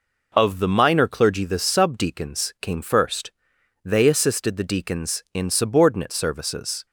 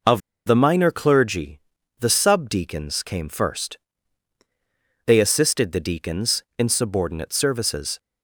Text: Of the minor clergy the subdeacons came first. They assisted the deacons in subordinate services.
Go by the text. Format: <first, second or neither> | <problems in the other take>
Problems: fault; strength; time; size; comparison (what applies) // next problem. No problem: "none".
first | pauses between "Of" and "the"; slight; at 0.1 s; 0.26 s long // pauses between "clergy" and "the"; at 1.5 s; 0.42 s long